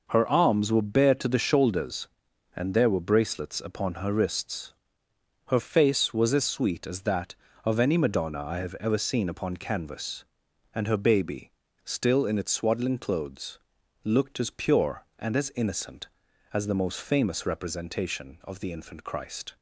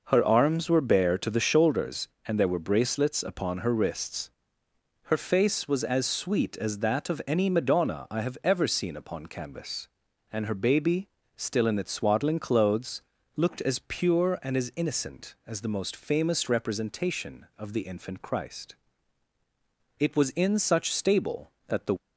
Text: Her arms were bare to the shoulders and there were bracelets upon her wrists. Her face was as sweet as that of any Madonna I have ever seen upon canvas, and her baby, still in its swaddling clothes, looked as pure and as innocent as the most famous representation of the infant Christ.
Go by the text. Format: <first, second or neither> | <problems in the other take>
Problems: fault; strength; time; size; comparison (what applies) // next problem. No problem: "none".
first | goes on to say "It was in such stable that the"; strong; from 19.9 s on; 1.9 s long